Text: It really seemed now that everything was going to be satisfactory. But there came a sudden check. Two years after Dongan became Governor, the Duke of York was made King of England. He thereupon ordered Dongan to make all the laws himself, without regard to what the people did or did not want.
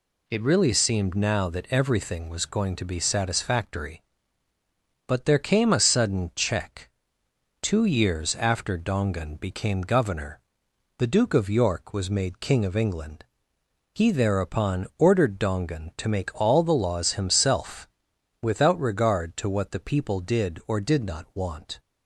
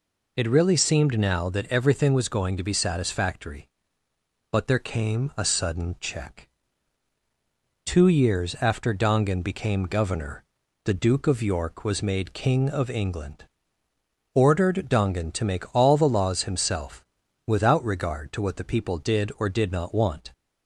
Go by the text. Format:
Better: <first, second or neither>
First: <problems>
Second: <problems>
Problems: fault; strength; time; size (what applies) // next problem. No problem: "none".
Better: first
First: none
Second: skips "He thereupon"; at 13.8 s